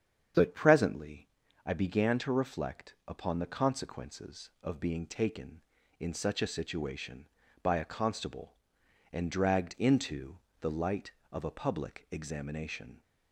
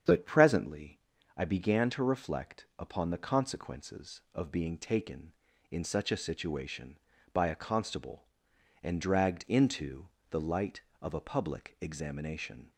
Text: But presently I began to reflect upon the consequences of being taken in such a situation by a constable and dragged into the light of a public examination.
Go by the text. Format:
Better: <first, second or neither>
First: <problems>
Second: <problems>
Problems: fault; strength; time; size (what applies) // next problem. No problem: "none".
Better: neither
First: starts louder than the rest; strong; until 1.7 s; 8 dB // pauses between "presently" and "I"; slight; at 1.2 s; 0.36 s long // pauses between "into" and "the"; slight; at 10.3 s; 0.20 s long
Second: starts louder than the rest; strong; until 1.4 s; 8 dB // pauses between "presently" and "I"; slight; at 1.0 s; 0.36 s long // pauses between "into" and "the"; slight; at 10.0 s; 0.20 s long